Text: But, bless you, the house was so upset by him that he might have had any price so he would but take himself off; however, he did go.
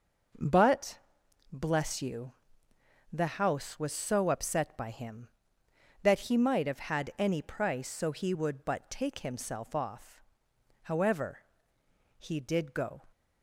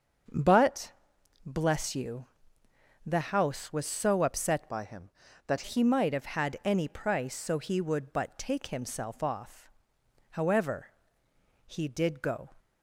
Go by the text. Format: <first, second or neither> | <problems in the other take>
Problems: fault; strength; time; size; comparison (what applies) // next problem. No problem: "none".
first | starts louder than the rest; until 1.8 s; 6.5 dB // changes voice from "by" to "that"; from 4.6 to 5.6 s; 1.0 s long